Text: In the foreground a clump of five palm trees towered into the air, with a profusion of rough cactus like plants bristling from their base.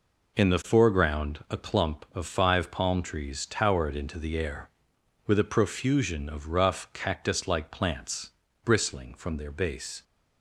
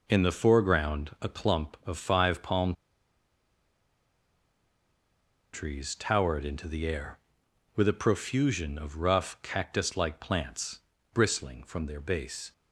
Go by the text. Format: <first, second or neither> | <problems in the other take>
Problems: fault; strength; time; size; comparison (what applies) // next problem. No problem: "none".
first | pauses between "palm" and "trees"; strong; at 2.7 s; 2.8 s long // pauses between "plants" and "bristling"; slight; at 10.8 s; 0.32 s long; slight in the first